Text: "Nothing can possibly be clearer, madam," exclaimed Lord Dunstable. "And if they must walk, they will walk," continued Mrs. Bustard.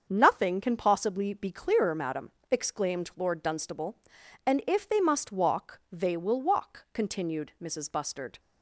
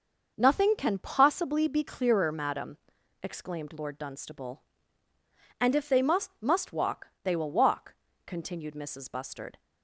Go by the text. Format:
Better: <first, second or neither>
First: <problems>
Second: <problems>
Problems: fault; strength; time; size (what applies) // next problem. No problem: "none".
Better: first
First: starts louder than the rest; until 1.1 s; 7 dB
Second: starts louder than the rest; until 1.3 s; 6 dB // says "must" twice; at 6.4 s